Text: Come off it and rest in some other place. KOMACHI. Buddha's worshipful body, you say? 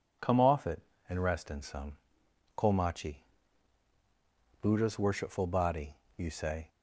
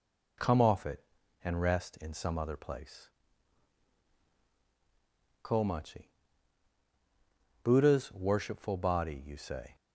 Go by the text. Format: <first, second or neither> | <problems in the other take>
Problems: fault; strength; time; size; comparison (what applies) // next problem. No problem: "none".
second | skips "other place"; at 2.2 s